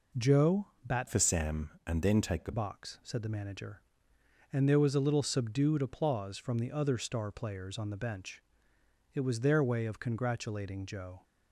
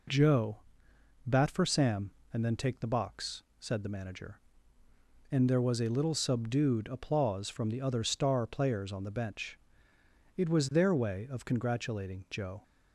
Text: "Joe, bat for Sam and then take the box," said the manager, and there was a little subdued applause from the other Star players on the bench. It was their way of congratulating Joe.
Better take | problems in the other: second | changes voice from "for" to "the"; from 1.0 to 2.5 s; 1.5 s long

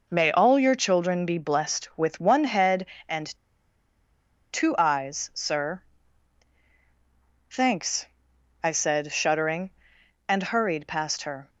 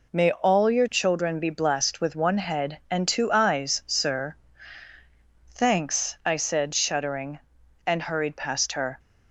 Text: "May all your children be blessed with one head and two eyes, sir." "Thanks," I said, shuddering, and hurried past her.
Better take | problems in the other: second | pauses between "and" and "two"; strong; at 3.2 s; 1.2 s long

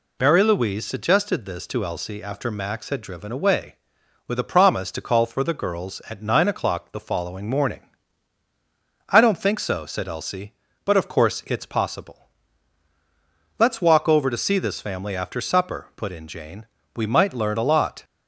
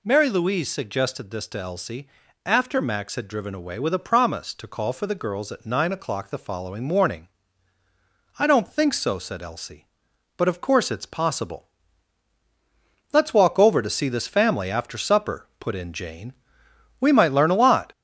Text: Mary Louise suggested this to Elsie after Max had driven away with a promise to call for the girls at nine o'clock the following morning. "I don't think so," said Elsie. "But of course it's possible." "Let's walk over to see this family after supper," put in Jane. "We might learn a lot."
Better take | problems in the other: first | gets louder; noticeable; throughout; 4 dB // pauses between "Elsie" and "after"; at 2.0 s; 0.38 s long

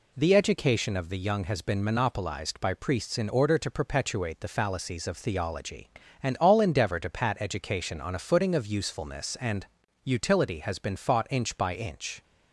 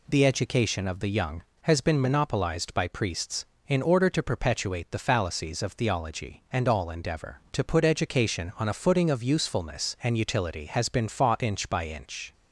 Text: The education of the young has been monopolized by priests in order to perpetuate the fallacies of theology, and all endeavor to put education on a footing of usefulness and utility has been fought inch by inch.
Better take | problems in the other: second | says "pat" for "put"; at 7.0 s // pauses between "and" and "utility"; at 9.6 s; 0.40 s long

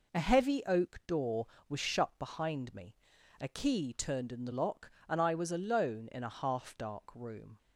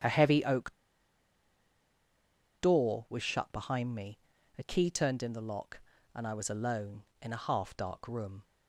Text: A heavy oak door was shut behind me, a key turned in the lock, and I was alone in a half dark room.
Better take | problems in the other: first | starts louder than the rest; strong; until 2.9 s; 9 dB // pauses between "oak" and "door"; strong; at 0.7 s; 1.8 s long

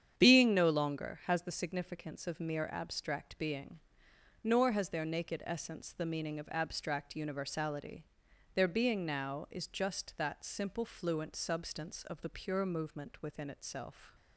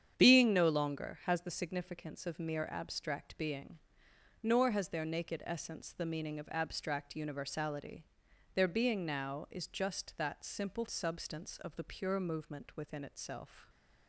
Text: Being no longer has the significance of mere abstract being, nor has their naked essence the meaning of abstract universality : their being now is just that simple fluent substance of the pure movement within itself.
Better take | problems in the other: first | starts louder than the rest; strong; until 1.1 s; 8.5 dB; strong in the first // skips "fluent"; at 10.8 s

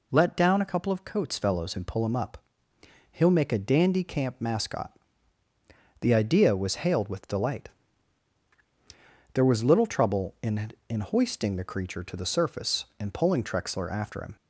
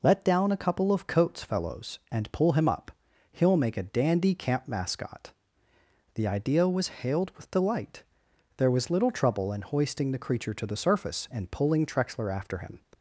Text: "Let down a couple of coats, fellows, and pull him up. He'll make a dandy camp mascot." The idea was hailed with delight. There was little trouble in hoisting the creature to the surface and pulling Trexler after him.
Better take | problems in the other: second | says "in" twice; at 10.8 s

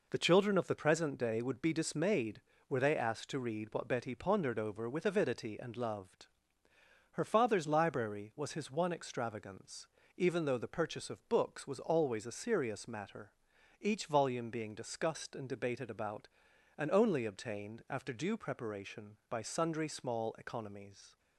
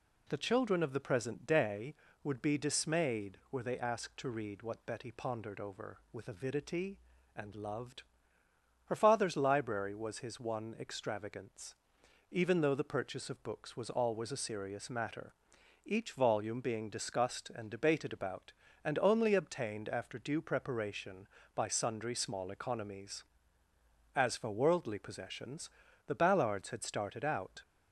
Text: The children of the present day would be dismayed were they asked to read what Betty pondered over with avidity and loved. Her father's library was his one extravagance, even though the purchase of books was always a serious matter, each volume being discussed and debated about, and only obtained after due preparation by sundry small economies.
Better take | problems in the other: first | goes on to say "As for worldly possessions the Ballards had started out"; strong; from 24.1 s on; 3.4 s long

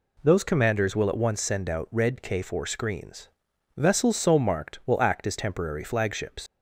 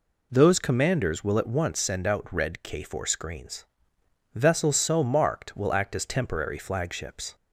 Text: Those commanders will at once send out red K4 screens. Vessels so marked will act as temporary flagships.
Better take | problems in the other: second | leaves "flagships" unfinished; at 6.4 s; 90 ms

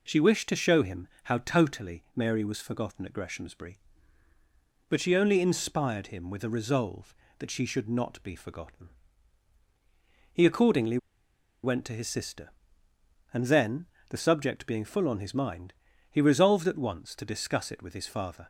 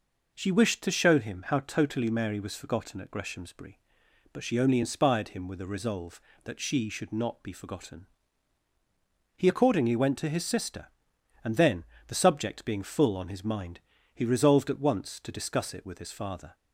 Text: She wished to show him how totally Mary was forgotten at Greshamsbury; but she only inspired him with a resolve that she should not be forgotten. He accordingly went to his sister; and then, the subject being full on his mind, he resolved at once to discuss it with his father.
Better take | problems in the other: second | pauses between "him" and "how"; slight; at 1.0 s; 0.16 s long // pauses between "accordingly" and "went"; noticeable; at 10.9 s; 0.66 s long

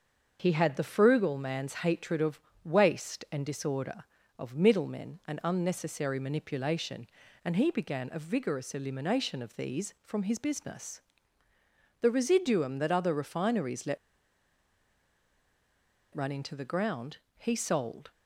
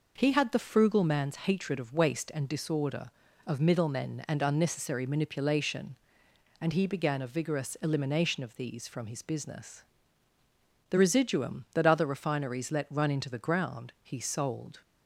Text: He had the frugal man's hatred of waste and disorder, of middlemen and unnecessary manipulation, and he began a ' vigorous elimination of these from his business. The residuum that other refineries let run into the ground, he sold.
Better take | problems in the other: second | starts louder than the rest; until 1.4 s; 6.5 dB // pauses between "of" and "waste"; slight; at 2.4 s; 0.24 s long // pauses between "let" and "run"; strong; at 13.9 s; 2.1 s long

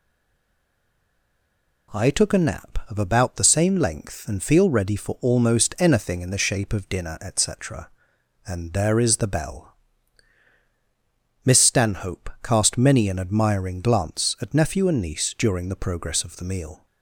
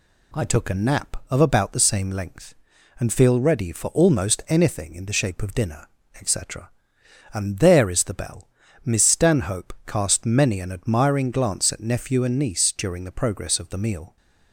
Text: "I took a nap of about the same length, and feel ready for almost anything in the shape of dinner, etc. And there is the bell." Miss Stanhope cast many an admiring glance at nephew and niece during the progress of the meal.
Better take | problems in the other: second | stays silent before the first word; noticeable; until 1.9 s; 1.9 s long

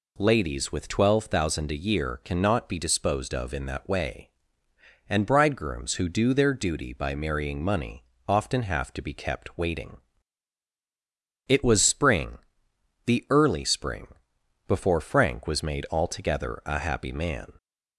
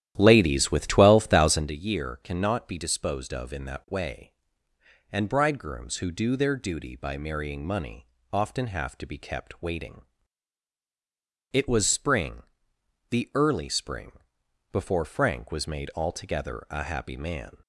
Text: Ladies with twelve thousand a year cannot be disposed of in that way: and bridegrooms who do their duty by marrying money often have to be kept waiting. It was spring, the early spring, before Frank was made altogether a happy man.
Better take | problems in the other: first | starts louder than the rest; strong; until 1.7 s; 11.5 dB // pauses between "money" and "often"; slight; at 8.0 s; 0.24 s long; slight in the first

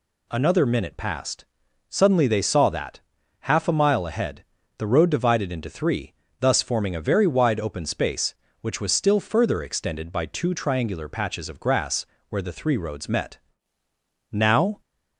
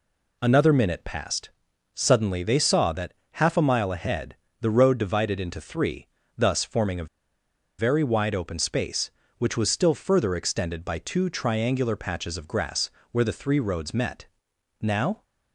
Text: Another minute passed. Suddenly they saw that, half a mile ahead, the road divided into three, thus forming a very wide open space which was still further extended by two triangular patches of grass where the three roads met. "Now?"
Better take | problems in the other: first | pauses between "a" and "very"; noticeable; at 7.0 s; 0.72 s long // pauses between "grass" and "where"; slight; at 12.9 s; 0.22 s long; slight in the first

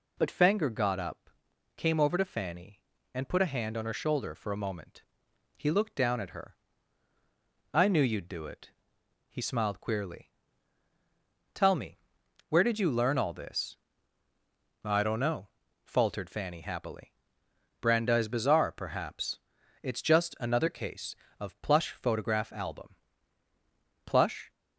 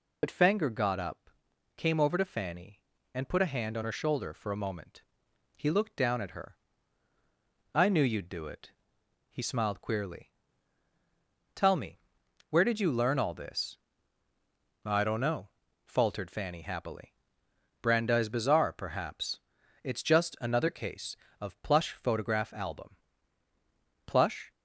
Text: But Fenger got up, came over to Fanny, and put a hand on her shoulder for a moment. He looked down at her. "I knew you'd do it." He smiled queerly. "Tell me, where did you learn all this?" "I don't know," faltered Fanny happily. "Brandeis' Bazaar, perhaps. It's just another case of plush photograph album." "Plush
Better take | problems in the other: first | loses the start of "But"; at 0.2 s; 50 ms

